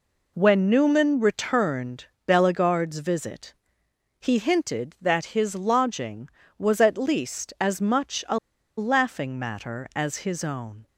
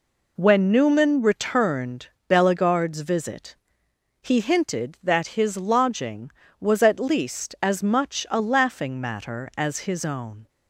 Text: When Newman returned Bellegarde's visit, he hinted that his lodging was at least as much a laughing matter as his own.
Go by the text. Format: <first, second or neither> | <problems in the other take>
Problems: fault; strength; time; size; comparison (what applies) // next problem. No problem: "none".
second | pauses between "returned" and "Bellegarde's"; slight; at 2.0 s; 0.20 s long; slight in the second // pauses between "a" and "laughing"; at 8.3 s; 0.40 s long